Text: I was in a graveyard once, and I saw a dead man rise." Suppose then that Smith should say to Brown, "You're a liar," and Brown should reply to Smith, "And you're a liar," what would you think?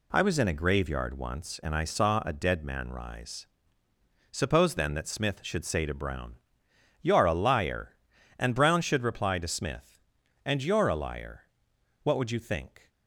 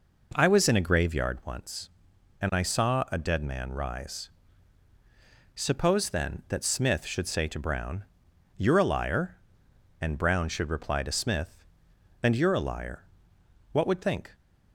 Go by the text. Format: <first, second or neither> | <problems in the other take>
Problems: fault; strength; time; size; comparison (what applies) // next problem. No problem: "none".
first | skips "you"; at 14.0 s